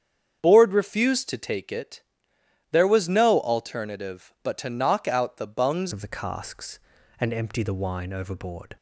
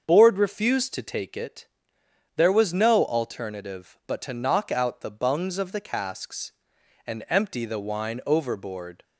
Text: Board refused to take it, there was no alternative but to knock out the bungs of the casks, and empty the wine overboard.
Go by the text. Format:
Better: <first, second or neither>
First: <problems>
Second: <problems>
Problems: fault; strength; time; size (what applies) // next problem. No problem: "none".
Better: second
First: starts louder than the rest; strong; until 1.4 s; 8 dB // changes voice at "of"; from 5.9 s on; 2.8 s long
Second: starts louder than the rest; until 1.0 s; 6.5 dB